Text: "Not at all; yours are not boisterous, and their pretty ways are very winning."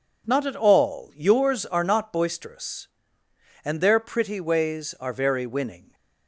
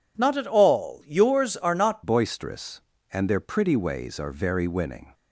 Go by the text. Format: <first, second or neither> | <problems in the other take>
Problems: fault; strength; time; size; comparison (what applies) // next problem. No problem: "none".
first | changes voice at "boisterous"; from 2.0 s on; 3.1 s long